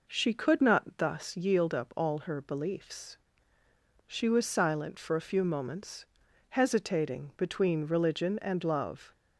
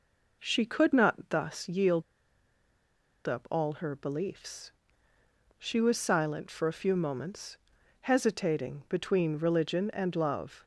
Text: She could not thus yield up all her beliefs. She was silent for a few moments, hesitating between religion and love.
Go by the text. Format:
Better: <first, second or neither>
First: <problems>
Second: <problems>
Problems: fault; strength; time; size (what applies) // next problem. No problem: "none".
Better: first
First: none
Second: pauses between "yield" and "up"; strong; at 2.0 s; 1.2 s long